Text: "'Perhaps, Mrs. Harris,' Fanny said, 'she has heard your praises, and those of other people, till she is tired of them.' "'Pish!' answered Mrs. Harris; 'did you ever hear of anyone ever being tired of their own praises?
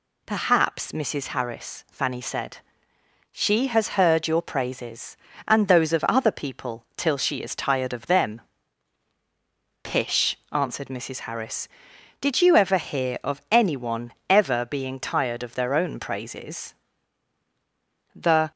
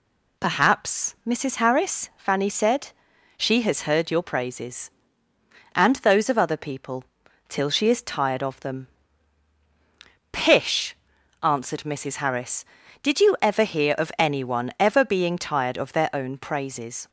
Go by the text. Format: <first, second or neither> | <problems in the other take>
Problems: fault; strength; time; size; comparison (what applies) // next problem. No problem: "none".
second | pauses between "anyone" and "ever"; slight; at 14.1 s; 0.16 s long // goes on to say "The"; slight; from 18.1 s on; 0.36 s long